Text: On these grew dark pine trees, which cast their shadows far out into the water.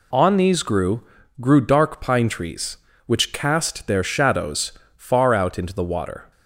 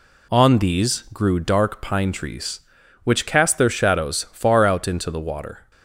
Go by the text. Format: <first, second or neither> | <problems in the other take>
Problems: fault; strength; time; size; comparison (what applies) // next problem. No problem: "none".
second | says "grew" twice; at 1.3 s // pauses between "shadows" and "far"; slight; at 4.7 s; 0.24 s long